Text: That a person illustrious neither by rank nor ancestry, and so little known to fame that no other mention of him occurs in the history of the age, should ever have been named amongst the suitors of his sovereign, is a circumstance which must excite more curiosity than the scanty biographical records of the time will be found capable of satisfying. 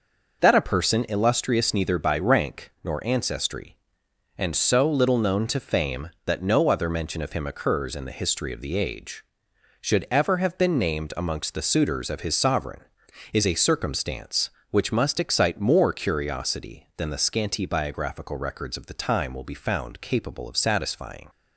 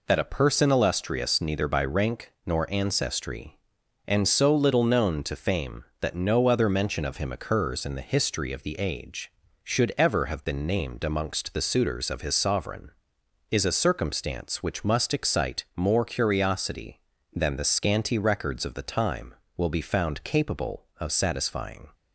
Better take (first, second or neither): first